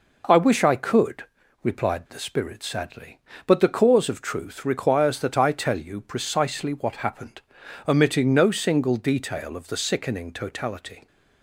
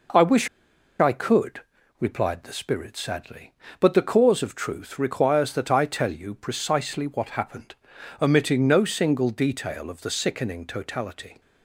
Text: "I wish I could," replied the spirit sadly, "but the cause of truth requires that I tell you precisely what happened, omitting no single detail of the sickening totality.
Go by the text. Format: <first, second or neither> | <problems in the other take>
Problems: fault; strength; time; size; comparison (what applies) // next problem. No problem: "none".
first | pauses between "wish" and "I"; noticeable; at 0.4 s; 0.52 s long